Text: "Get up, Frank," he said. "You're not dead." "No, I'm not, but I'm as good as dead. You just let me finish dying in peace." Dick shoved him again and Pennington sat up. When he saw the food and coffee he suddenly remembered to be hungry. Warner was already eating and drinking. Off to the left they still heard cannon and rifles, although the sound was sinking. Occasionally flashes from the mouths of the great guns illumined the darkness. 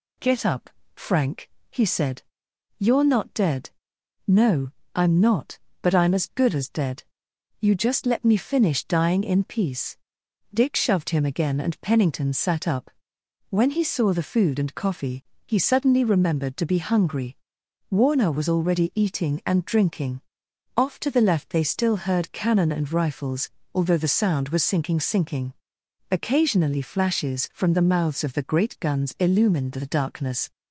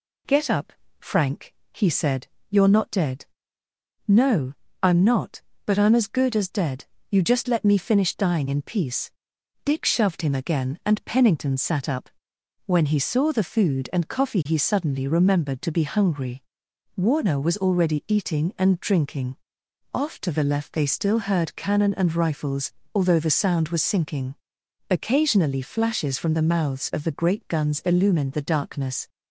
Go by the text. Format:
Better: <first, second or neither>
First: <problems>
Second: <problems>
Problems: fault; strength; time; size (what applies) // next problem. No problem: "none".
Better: second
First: pauses between "coffee" and "he"; slight; at 15.2 s; 0.24 s long // says "sinking" twice; at 25.0 s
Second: none